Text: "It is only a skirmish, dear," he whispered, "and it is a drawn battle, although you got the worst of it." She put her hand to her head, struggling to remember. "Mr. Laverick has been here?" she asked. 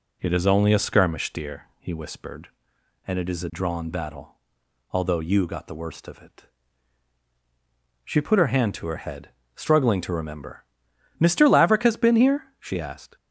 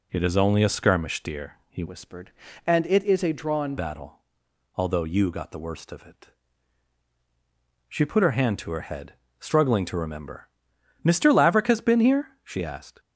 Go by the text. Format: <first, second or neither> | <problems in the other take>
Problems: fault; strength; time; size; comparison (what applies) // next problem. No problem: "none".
first | changes voice from "whispered" to "drawn"; from 1.8 to 3.7 s; 1.9 s long